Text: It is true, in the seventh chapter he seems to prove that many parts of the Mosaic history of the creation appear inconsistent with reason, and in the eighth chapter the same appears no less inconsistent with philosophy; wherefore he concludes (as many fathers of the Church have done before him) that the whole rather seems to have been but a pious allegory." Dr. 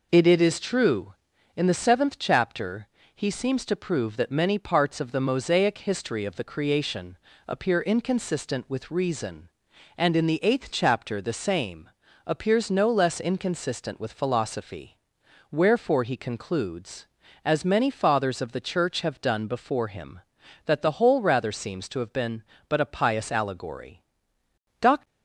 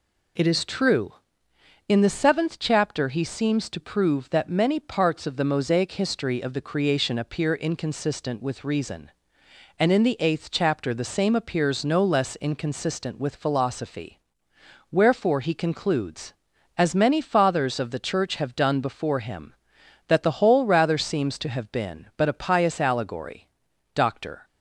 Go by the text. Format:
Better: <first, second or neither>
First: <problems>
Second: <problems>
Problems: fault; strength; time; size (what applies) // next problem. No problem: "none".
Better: second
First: says "It" twice; at 0.2 s // pauses between "chapter" and "he"; slight; at 2.8 s; 0.28 s long // pauses between "creation" and "appear"; slight; at 7.1 s; 0.28 s long // pauses between "same" and "appears"; slight; at 11.9 s; 0.34 s long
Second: none